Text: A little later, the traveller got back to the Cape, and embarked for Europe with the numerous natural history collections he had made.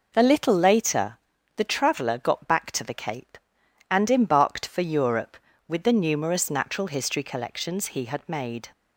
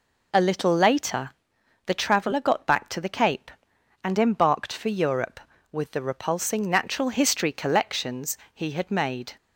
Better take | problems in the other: first | says "repulsing" for "numerous"; at 6.0 s // pauses between "collections" and "he"; slight; at 8.3 s; 0.18 s long

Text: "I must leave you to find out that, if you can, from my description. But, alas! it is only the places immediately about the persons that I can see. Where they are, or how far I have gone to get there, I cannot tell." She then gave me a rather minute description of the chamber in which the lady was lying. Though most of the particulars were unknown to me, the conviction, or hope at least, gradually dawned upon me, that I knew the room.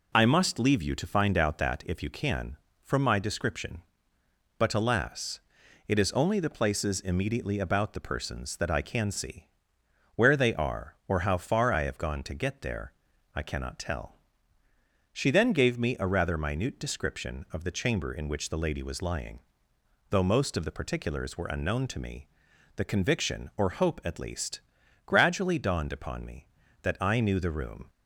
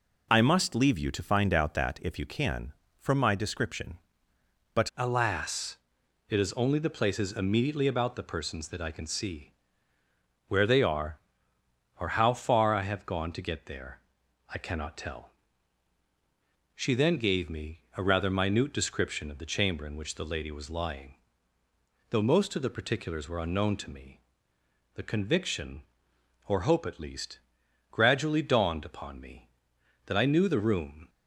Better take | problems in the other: first | changes voice at "alas"; from 4.9 s on; 26.1 s long

